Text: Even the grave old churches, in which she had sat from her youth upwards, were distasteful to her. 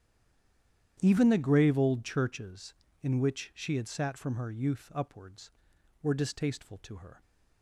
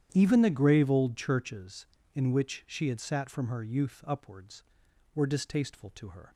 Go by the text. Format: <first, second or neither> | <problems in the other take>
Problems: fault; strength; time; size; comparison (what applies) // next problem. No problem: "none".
second | stays silent before the first word; until 0.9 s; 0.9 s long // starts louder than the rest; strong; until 2.0 s; 10 dB; strong in the second